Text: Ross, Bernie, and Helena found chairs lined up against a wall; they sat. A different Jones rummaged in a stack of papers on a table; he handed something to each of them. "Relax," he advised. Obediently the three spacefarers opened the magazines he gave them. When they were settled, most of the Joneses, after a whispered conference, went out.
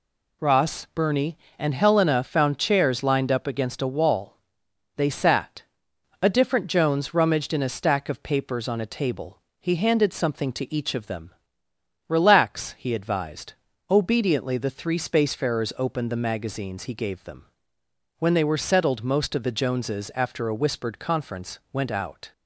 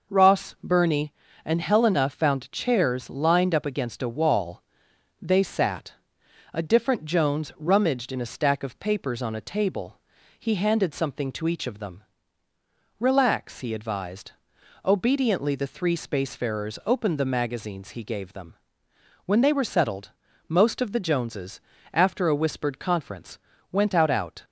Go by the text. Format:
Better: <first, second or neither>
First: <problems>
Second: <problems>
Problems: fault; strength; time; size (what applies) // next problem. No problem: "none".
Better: first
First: none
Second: says "out" twice; at 24.1 s